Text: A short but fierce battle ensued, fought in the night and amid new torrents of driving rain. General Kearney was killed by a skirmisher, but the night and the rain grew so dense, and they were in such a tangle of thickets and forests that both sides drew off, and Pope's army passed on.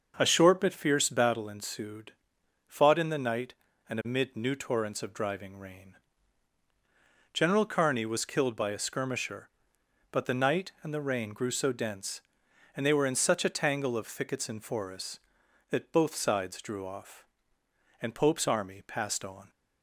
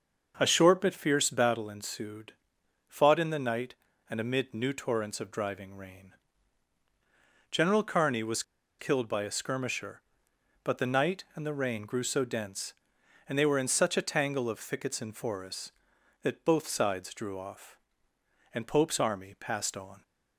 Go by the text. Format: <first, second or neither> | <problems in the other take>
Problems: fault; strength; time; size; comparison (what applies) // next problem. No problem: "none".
first | starts louder than the rest; noticeable; until 1.3 s; 6 dB; noticeable in the first // pauses between "was" and "killed"; at 8.4 s; 0.37 s long